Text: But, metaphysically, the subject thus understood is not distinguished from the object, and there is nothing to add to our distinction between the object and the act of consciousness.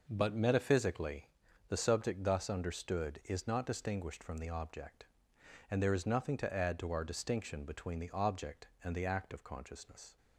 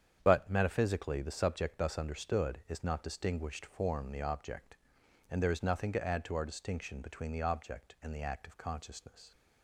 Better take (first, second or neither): first